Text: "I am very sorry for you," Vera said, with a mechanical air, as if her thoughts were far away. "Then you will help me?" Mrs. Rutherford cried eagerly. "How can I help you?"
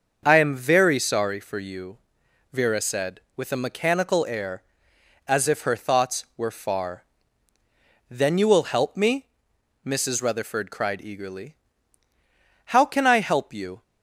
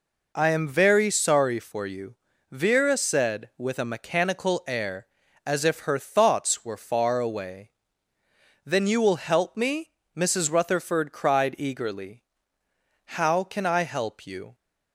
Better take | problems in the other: second | starts louder than the rest; until 1.2 s; 6.5 dB // skips "away"; at 7.5 s

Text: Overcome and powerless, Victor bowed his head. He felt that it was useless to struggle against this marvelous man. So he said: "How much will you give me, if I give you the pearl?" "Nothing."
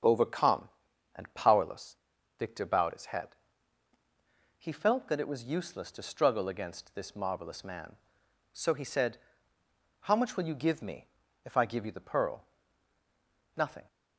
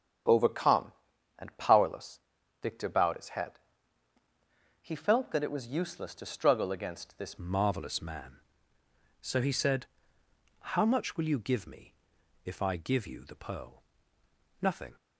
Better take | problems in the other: first | starts louder than the rest; strong; until 1.7 s; 8.5 dB; strong in the first // changes voice at "marvelous"; from 7.3 s on; 7.6 s long

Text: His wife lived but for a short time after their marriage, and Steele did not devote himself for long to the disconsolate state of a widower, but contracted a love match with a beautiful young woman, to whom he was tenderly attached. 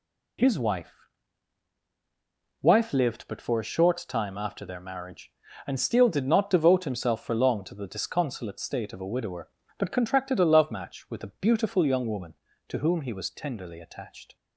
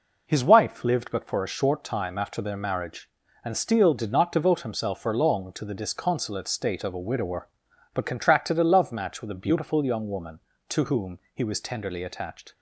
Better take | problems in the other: second | says "wife" twice; at 2.6 s

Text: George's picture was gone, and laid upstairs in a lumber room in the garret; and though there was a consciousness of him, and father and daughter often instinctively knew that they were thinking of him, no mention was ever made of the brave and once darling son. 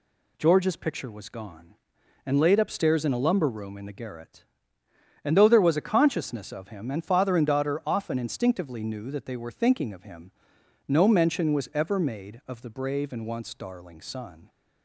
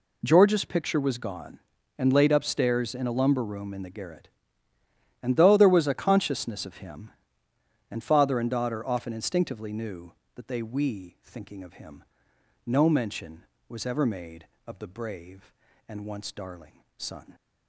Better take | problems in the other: first | says "we" for "were"; at 10.6 s // pauses between "darling" and "son"; slight; at 16.8 s; 0.16 s long

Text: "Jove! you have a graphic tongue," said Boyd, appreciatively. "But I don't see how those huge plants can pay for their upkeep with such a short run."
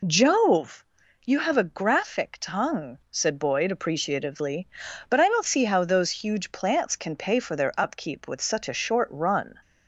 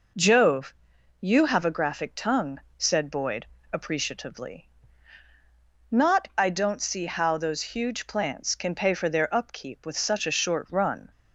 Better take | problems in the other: first | says "Not" for "But"; at 5.9 s

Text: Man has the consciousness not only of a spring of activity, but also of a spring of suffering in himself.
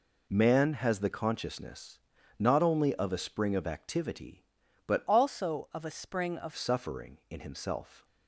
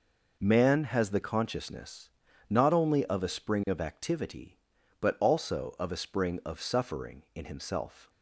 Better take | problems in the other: second | pauses between "consciousness" and "not"; at 1.9 s; 0.40 s long; also in the second // changes voice from "also" to "of"; from 5.0 to 6.5 s; 1.5 s long

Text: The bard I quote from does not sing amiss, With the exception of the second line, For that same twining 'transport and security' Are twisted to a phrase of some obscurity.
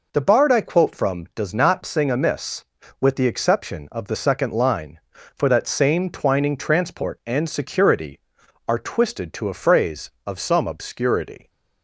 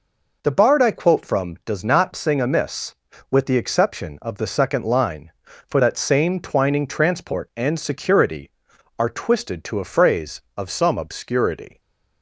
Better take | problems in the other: neither | none

